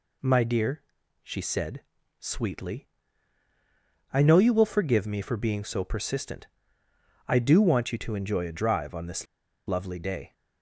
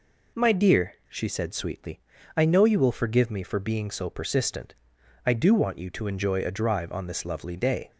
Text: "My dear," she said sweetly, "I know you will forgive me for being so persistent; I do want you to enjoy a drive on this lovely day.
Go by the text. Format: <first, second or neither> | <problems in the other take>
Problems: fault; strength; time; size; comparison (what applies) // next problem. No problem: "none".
second | pauses between "said" and "sweetly"; at 1.8 s; 0.38 s long // pauses between "this" and "lovely"; at 9.2 s; 0.42 s long